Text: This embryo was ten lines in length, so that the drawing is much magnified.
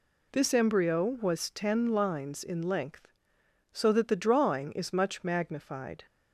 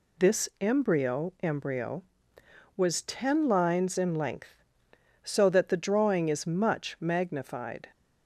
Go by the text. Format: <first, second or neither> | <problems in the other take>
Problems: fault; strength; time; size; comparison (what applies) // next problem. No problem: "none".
first | says "embryo" twice; at 1.4 s